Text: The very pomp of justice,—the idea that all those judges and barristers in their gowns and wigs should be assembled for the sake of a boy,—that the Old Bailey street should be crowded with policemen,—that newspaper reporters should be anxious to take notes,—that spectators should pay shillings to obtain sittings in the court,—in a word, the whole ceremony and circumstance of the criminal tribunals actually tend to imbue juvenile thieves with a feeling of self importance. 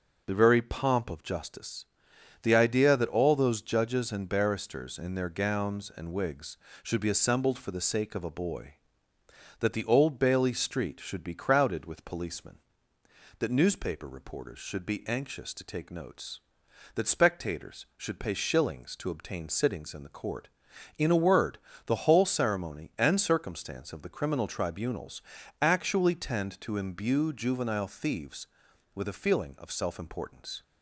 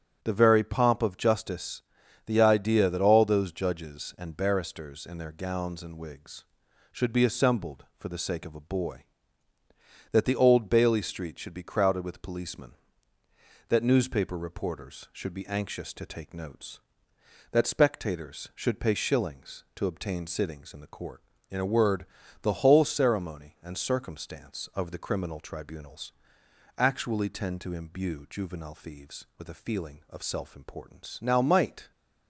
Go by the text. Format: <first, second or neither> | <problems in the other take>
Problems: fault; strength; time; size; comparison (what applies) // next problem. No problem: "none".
first | starts louder than the rest; strong; until 1.2 s; 8.5 dB // pauses between "tribunals" and "actually"; noticeable; at 26.1 s; 0.64 s long; also in the first // goes on to say "Now might"; noticeable; from 31.2 s on; 0.70 s long